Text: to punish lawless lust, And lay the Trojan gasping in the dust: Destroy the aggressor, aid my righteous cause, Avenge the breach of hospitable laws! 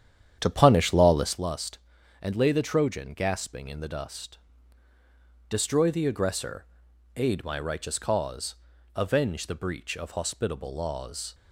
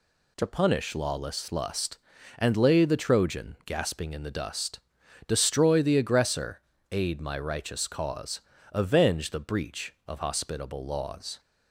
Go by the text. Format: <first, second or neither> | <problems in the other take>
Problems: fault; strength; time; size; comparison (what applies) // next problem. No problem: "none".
second | starts louder than the rest; strong; until 1.4 s; 9.5 dB